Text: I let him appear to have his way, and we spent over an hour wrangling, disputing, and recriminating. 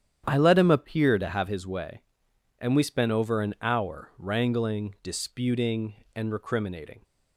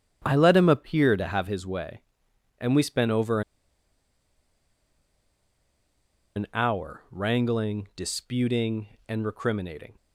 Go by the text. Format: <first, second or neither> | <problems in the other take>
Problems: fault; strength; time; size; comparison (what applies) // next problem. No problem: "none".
first | starts louder than the rest; strong; until 1.2 s; 9.5 dB; strong in the first // pauses between "over" and "an"; strong; at 3.4 s; 2.9 s long